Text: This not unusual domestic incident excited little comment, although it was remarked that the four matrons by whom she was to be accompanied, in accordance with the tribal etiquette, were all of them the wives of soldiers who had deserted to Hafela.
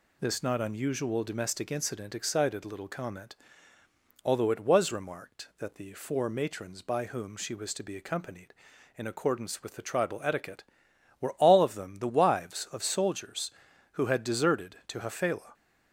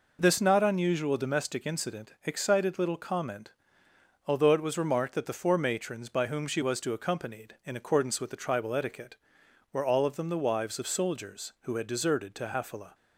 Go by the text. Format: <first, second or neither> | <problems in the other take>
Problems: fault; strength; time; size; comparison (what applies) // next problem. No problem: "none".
first | skips "be"; at 6.9 s